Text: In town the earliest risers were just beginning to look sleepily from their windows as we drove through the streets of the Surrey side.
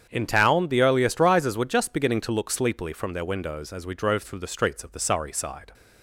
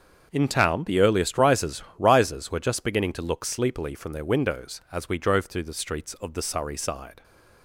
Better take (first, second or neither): first